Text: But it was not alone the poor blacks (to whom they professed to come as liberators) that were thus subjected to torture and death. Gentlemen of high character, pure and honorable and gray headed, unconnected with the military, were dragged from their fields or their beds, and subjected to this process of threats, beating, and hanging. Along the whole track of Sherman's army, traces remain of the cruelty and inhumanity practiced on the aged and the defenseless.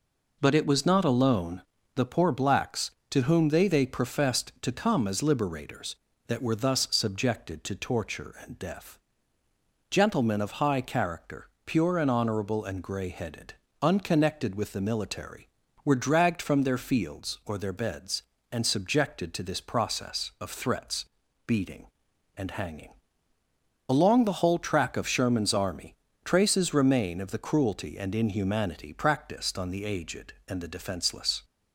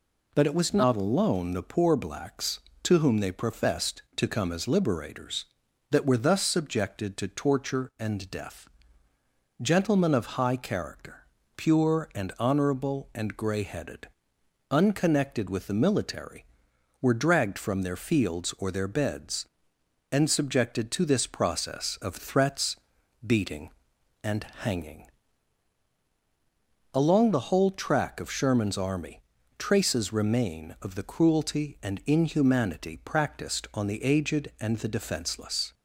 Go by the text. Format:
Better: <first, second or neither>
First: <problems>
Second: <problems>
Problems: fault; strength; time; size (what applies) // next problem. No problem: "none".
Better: second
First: pauses between "alone" and "the"; slight; at 1.6 s; 0.34 s long // says "they" twice; at 3.6 s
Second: none